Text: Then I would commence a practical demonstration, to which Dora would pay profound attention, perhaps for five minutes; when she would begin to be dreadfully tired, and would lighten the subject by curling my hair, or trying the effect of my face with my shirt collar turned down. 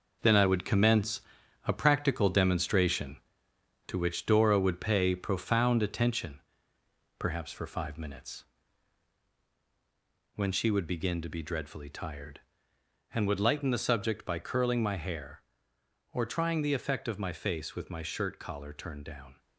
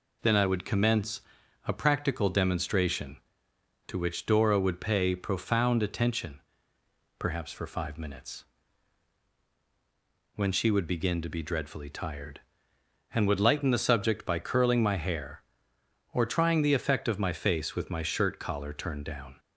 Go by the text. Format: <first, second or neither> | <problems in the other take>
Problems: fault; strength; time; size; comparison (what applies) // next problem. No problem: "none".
second | gets quieter; strong; throughout; 8 dB // pauses between "commence" and "a"; noticeable; at 1.2 s; 0.46 s long; noticeable in the second